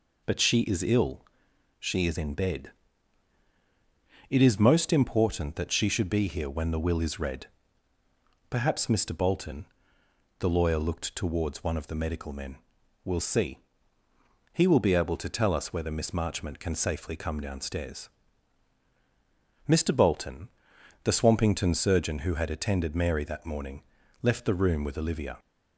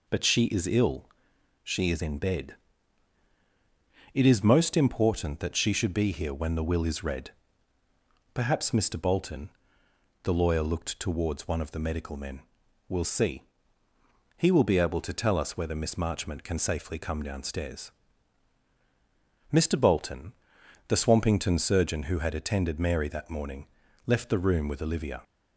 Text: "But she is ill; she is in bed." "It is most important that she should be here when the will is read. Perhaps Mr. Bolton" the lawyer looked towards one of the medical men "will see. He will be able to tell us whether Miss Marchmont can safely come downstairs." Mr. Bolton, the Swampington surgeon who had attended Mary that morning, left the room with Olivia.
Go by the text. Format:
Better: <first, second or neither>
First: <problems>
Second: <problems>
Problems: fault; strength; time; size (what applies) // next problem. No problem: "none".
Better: neither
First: pauses between "Bolton" and "the"; noticeable; at 9.6 s; 0.72 s long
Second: pauses between "Bolton" and "the"; noticeable; at 9.5 s; 0.72 s long